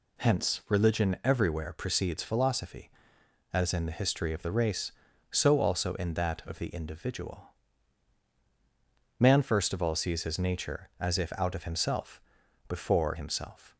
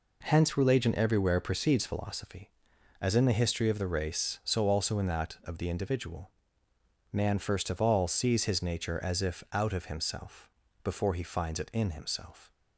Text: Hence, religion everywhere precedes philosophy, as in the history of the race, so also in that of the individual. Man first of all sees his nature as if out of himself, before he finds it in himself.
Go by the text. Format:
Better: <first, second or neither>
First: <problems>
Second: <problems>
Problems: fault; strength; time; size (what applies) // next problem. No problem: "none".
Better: second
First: skips "he finds it in"; at 13.1 s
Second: none